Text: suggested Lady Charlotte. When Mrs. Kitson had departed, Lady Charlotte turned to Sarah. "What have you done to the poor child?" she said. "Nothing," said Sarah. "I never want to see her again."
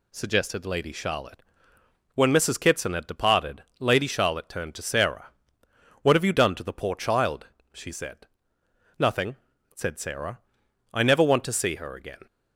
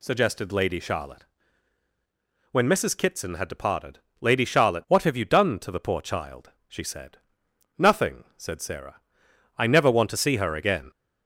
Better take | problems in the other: first | skips "turned to Sarah"; at 4.8 s

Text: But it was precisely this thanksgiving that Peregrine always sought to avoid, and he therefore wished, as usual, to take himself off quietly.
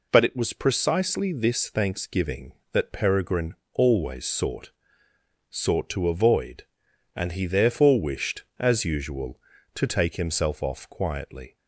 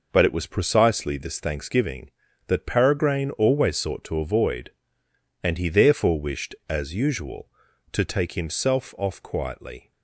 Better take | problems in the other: second | pauses between "Peregrine" and "always"; slight; at 3.5 s; 0.18 s long // says "sought" twice; at 5.4 s

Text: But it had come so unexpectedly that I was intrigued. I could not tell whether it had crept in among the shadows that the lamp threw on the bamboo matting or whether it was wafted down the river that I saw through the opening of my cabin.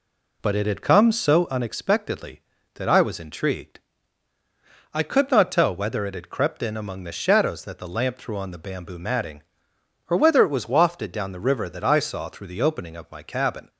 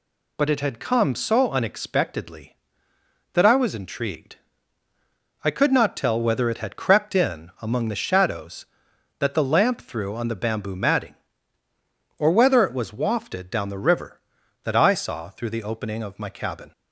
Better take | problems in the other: second | starts louder than the rest; slight; until 1.6 s; 3 dB

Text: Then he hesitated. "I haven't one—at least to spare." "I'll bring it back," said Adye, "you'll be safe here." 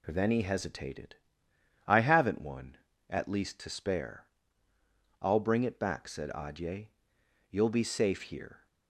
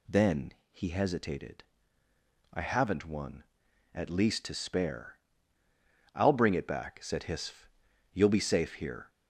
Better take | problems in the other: first | pauses between "Then" and "he"; slight; at 0.5 s; 0.20 s long // says "Hisf" for "Adye"; at 7.2 s

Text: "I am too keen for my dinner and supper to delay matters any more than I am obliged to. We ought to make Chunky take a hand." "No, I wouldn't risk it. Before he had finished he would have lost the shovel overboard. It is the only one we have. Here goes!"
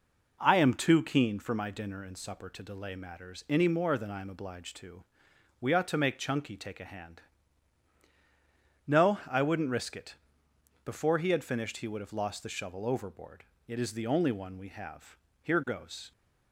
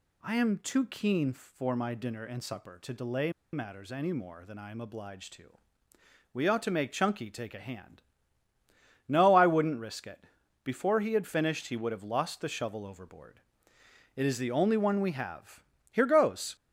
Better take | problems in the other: first | pauses between "delay" and "matters"; slight; at 3.3 s; 0.22 s long

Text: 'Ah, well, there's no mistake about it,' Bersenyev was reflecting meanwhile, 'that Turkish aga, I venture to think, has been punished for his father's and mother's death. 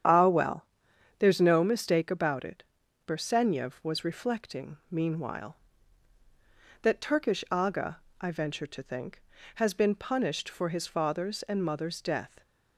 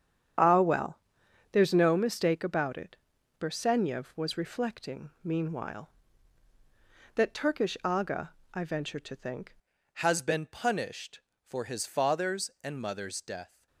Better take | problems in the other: first | starts louder than the rest; strong; until 1.9 s; 8.5 dB; strong in the first // changes voice at "has"; from 9.9 s on; 3.7 s long

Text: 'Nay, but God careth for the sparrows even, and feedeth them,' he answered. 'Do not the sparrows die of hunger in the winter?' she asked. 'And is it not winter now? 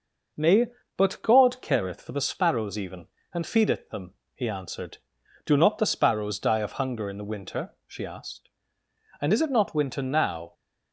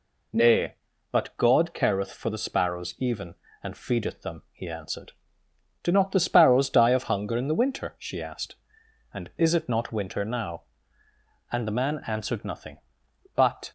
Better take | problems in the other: first | goes on to say "And the man answered nothing but"; strong; from 11.4 s on; 2.2 s long

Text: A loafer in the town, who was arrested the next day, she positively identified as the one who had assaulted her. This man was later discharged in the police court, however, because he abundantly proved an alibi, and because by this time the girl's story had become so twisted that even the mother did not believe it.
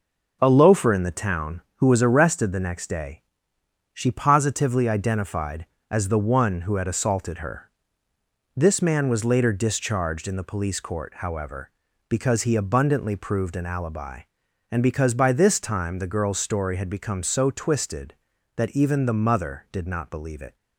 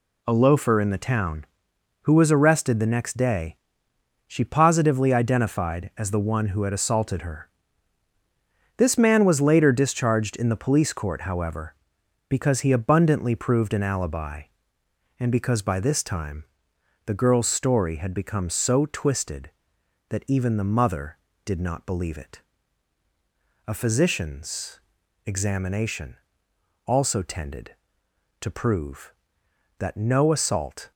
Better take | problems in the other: first | pauses between "time" and "the"; noticeable; at 16.4 s; 0.60 s long // goes on to say "A physician's examination also tended to prove that no assault"; strong; from 23.6 s on; 7.2 s long

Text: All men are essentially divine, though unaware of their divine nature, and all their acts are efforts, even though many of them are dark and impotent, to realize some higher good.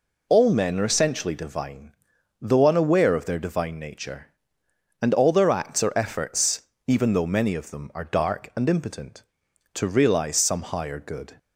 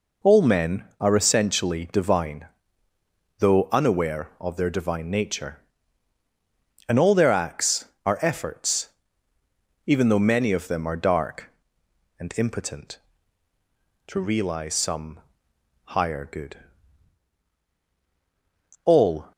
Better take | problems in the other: first | pauses between "some" and "higher"; noticeable; at 15.1 s; 0.66 s long // goes on to say "All"; slight; from 18.8 s on; 0.48 s long

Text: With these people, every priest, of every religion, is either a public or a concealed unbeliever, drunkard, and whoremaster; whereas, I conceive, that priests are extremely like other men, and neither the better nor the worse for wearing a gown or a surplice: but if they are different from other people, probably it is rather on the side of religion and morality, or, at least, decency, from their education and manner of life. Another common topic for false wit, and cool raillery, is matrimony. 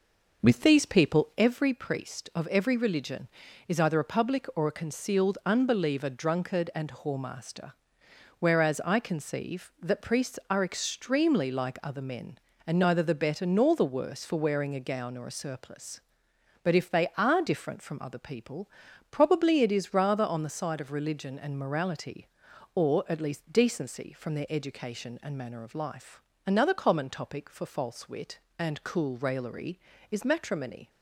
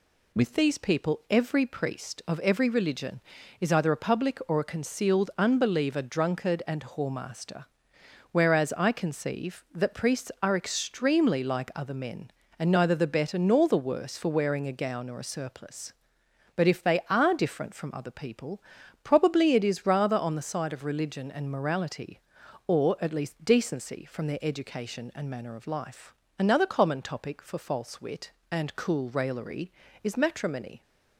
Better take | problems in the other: second | starts louder than the rest; noticeable; until 1.5 s; 5.5 dB

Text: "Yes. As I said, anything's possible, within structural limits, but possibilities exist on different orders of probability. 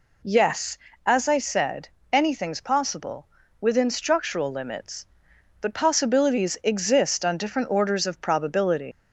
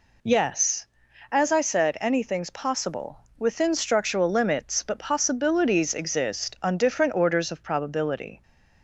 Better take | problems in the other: second | leaves "probability" unfinished; at 8.9 s; 130 ms

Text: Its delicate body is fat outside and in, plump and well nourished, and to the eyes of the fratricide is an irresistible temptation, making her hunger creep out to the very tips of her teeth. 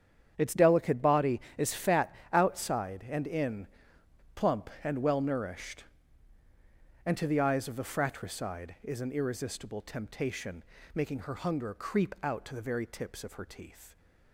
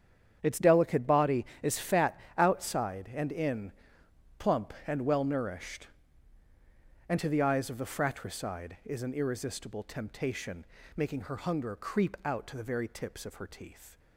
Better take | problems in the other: neither | starts louder than the rest; strong; the same in both // pauses between "fat" and "outside"; slight; the same in both

